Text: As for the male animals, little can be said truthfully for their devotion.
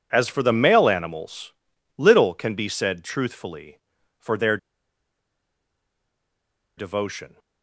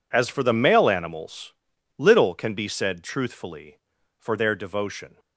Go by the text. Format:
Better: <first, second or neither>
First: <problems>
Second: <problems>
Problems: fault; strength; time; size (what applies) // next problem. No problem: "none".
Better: second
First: pauses between "their" and "devotion"; strong; at 4.5 s; 2.2 s long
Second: none